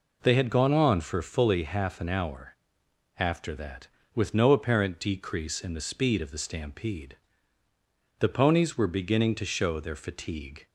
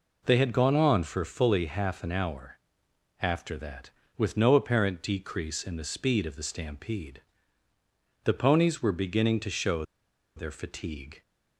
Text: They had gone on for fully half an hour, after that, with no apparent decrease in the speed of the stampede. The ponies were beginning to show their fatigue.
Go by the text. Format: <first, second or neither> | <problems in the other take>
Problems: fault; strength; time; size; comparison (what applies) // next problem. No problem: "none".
first | pauses between "show" and "their"; noticeable; at 9.8 s; 0.53 s long